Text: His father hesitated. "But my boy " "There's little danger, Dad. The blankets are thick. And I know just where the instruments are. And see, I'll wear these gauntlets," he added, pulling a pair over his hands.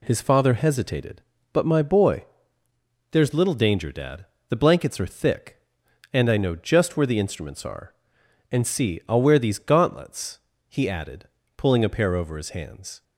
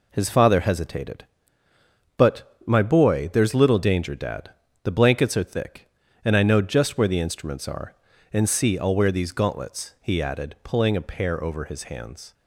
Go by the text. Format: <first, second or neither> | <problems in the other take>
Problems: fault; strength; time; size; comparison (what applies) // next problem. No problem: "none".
neither | none